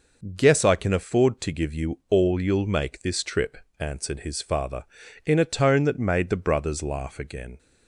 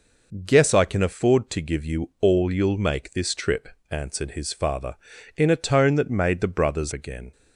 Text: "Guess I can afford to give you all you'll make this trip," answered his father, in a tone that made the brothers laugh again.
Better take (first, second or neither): first